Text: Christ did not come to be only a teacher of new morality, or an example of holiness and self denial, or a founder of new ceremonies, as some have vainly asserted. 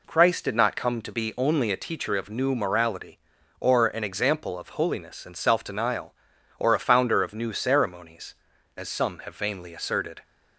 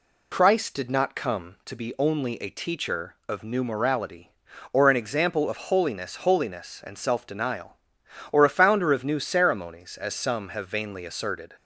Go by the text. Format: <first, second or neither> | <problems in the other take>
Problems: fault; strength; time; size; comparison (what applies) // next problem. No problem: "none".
first | says "holiness" twice; at 6.2 s